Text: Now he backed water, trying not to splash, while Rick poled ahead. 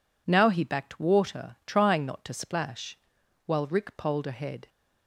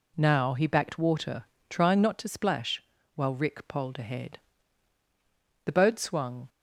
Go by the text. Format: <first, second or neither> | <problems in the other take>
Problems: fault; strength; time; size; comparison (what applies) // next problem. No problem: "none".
first | goes on to say "The boat swung"; noticeable; from 5.6 s on; 0.84 s long